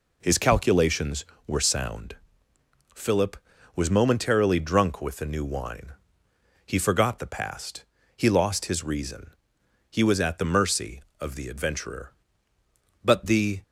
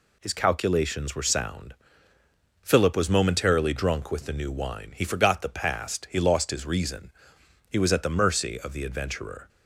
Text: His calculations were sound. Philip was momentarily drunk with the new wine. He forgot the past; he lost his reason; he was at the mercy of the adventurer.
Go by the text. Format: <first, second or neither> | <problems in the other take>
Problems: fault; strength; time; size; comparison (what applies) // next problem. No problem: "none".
second | goes on to say "But the"; from 13.0 s on; 0.58 s long